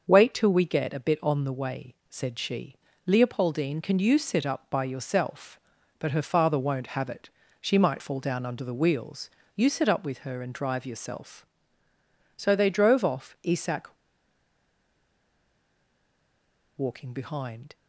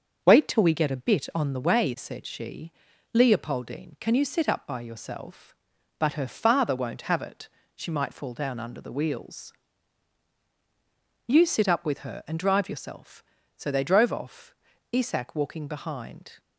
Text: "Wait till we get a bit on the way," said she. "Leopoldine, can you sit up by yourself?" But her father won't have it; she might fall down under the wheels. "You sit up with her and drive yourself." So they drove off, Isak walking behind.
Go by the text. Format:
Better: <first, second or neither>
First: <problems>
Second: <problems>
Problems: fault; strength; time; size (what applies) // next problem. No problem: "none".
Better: second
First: starts louder than the rest; until 1.0 s; 6 dB // pauses between "Isak" and "walking"; strong; at 13.9 s; 2.8 s long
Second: starts louder than the rest; until 1.2 s; 6.5 dB